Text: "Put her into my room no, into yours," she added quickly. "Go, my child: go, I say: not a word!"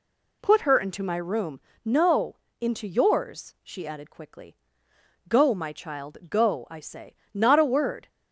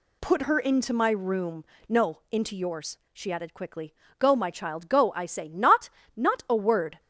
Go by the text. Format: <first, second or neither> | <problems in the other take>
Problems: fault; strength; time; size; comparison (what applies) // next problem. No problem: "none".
first | pauses between "room" and "no"; slight; at 1.6 s; 0.24 s long; slight in the first // says "not" twice; at 6.1 s